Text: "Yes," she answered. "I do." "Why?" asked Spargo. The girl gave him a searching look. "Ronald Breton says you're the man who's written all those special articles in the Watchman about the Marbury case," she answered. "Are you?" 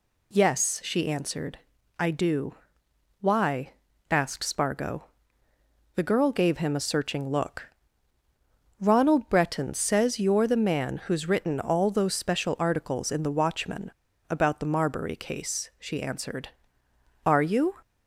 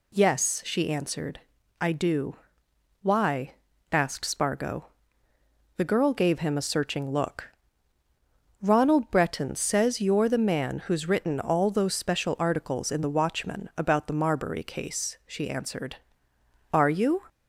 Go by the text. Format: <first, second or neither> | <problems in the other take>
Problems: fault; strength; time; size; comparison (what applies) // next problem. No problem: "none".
second | pauses between "Watchman" and "about"; at 13.9 s; 0.39 s long